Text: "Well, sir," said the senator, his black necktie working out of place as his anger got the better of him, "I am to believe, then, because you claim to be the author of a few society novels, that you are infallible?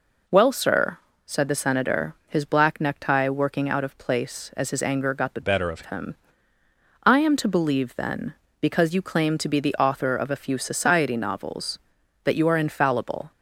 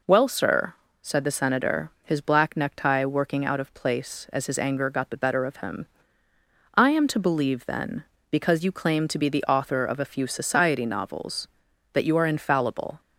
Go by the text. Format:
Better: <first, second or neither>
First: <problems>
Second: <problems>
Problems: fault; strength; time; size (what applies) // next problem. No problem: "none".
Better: second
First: changes voice from "better" to "of"; from 5.4 to 5.8 s; 0.4 s long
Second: none